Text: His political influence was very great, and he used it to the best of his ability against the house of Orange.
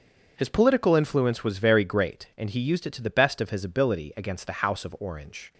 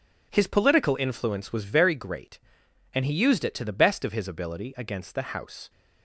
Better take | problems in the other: first | stops before "of Orange"; at 5.6 s

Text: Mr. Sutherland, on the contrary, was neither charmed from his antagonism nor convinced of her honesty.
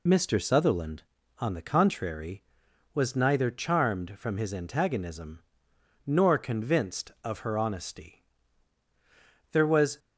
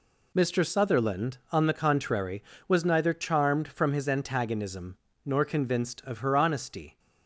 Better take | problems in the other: second | pauses between "antagonism" and "nor"; noticeable; at 5.4 s; 0.66 s long; slight in the second // goes on to say "There was"; slight; from 9.5 s on; 0.48 s long

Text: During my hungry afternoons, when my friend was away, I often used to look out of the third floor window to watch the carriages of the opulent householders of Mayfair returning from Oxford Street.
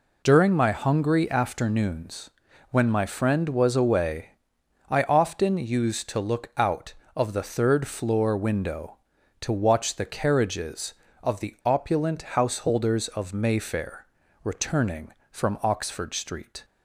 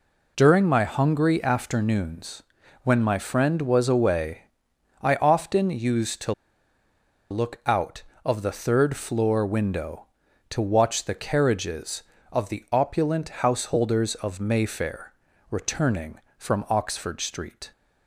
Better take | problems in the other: first | pauses between "to" and "look"; noticeable; at 6.3 s; 0.97 s long // pauses between "Mayfair" and "returning"; at 15.1 s; 0.38 s long; also in the first

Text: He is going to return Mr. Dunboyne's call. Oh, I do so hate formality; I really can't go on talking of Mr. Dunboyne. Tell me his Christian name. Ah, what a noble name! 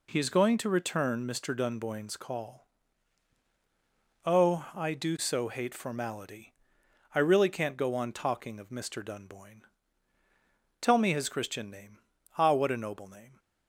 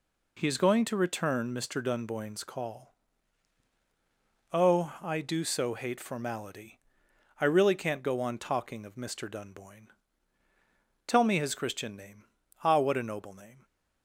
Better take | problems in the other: neither | none

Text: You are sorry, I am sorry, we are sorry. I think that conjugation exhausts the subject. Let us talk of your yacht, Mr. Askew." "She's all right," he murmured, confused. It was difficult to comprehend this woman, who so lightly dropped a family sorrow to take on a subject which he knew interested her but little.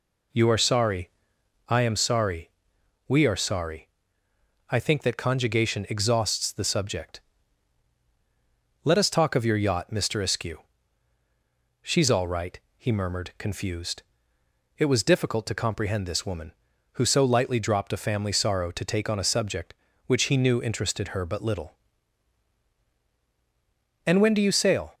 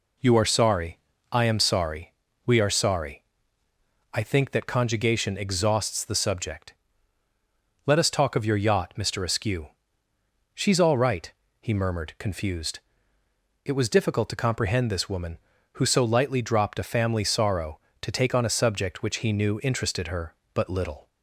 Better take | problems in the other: second | goes on to say "And when do you sail"; noticeable; from 24.0 s on; 0.88 s long

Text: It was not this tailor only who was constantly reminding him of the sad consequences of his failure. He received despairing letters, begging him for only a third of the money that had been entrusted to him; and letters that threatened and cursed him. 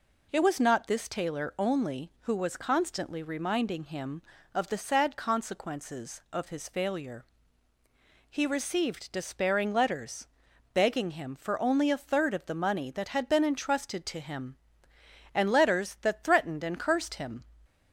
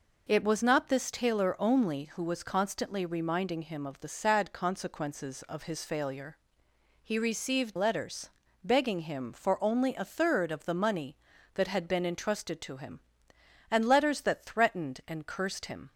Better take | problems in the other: first | skips "despairing"; at 7.7 s

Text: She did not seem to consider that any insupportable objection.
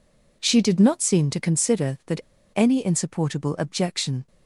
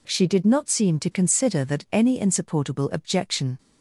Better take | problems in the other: second | pauses between "that" and "any"; slight; at 2.2 s; 0.34 s long

